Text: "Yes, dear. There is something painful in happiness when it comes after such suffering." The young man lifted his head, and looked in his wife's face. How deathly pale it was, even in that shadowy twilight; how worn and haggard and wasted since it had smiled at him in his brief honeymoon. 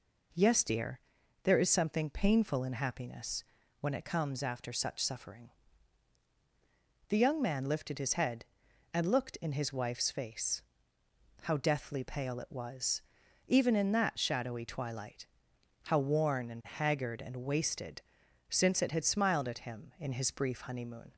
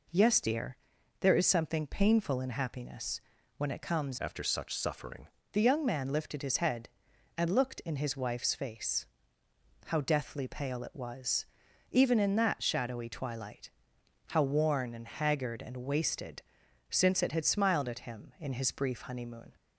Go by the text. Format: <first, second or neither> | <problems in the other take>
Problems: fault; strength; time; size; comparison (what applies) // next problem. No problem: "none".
first | pauses between "happiness" and "when"; at 3.2 s; 0.38 s long; also in the first // changes voice from "after" to "suffering"; from 4.1 to 5.2 s; 1.1 s long // pauses between "wasted" and "since"; noticeable; at 16.4 s; 0.48 s long; noticeable in the first